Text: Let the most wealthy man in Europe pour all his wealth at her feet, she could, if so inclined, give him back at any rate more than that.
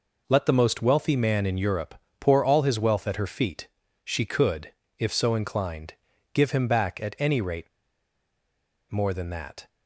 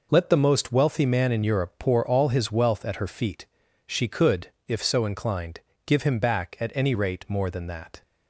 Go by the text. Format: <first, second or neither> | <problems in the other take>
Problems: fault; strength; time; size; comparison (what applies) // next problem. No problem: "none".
second | pauses between "Europe" and "pour"; slight; at 1.9 s; 0.26 s long // pauses between "rate" and "more"; at 7.6 s; 1.2 s long